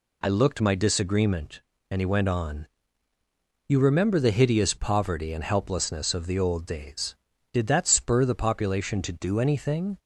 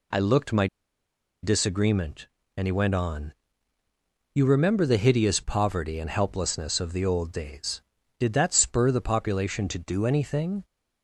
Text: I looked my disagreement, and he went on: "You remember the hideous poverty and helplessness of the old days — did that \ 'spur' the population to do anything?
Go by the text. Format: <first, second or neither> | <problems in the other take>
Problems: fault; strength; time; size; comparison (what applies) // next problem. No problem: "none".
first | pauses between "my" and "disagreement"; noticeable; at 0.6 s; 0.76 s long